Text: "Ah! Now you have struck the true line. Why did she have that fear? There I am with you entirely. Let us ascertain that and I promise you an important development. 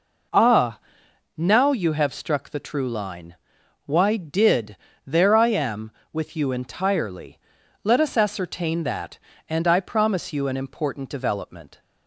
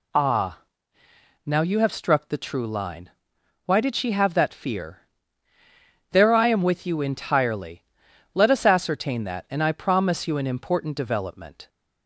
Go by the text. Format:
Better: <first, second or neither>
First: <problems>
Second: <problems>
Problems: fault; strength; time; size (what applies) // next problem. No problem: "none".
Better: second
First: skips "she have that fear"; at 4.9 s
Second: none